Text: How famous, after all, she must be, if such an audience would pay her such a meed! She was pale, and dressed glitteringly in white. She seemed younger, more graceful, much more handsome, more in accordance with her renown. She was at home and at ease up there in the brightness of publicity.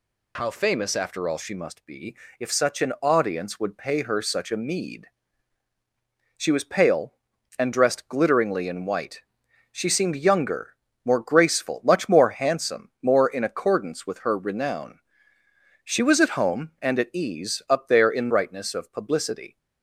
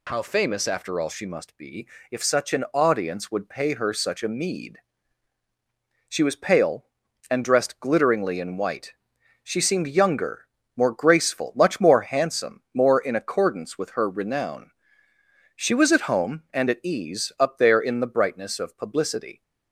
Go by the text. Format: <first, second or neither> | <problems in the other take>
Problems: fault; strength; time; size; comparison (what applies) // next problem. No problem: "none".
second | skips "the"; at 18.2 s